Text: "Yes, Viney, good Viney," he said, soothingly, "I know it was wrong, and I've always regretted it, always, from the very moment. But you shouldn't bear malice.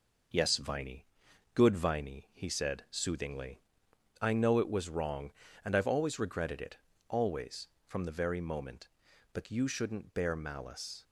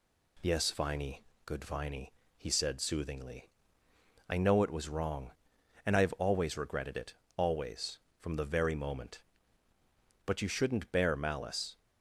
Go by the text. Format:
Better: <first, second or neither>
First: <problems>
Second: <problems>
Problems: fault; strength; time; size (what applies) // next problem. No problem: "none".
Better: second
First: gets quieter; noticeable; throughout; 4 dB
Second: none